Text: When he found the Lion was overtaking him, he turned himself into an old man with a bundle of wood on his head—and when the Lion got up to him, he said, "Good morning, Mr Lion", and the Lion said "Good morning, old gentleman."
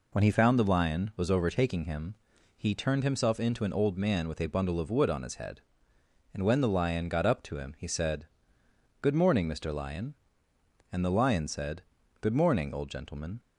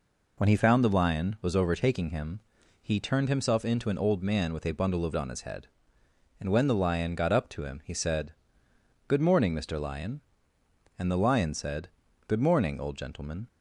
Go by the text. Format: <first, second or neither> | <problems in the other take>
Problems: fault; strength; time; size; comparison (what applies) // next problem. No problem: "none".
first | skips "wood"; at 5.1 s // pauses between "said" and "Good"; at 11.8 s; 0.40 s long; also in the first